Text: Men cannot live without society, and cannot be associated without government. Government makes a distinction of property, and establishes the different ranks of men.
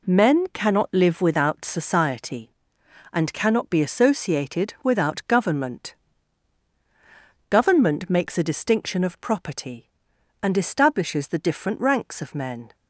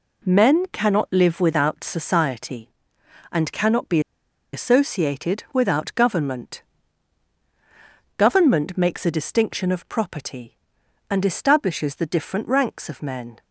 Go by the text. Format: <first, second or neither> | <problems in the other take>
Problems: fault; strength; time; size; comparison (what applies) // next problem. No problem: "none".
first | pauses between "be" and "associated"; noticeable; at 3.9 s; 0.53 s long